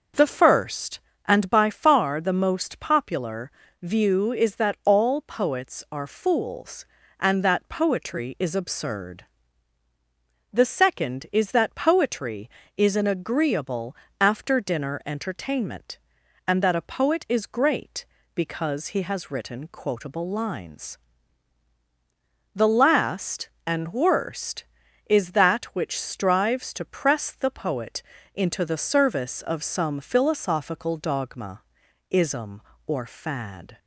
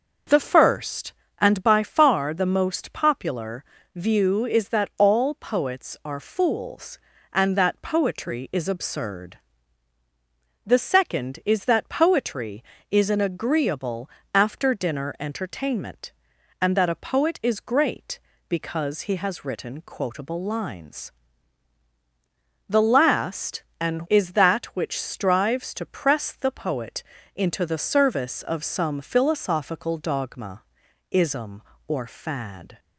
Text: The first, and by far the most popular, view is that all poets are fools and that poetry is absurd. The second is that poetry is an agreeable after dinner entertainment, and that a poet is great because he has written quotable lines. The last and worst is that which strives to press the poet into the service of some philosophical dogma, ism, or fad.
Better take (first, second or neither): first